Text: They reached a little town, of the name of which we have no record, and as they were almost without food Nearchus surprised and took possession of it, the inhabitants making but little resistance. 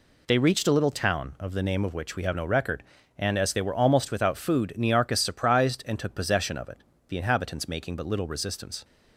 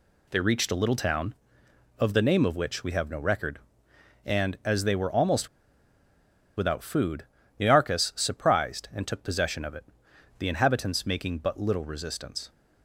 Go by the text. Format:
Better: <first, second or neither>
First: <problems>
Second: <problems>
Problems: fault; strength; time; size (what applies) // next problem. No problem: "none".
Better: first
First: none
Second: pauses between "almost" and "without"; at 5.4 s; 1.0 s long // pauses between "food" and "Nearchus"; slight; at 7.2 s; 0.36 s long